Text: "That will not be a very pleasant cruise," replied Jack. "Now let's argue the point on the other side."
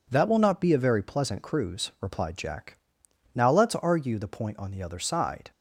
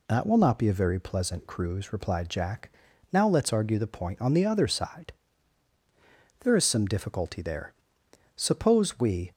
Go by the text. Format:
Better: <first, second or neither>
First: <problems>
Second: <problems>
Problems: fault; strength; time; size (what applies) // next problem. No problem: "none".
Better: first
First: none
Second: goes on to say "There is some difficulty there suppose we"; strong; from 6.4 s on; 2.9 s long